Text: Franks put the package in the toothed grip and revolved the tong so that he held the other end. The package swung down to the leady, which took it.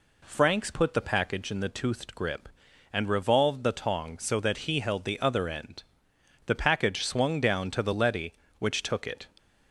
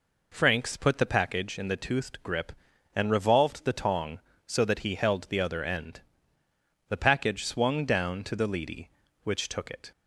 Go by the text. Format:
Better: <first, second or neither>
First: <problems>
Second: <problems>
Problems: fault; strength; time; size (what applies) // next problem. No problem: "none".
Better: neither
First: none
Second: none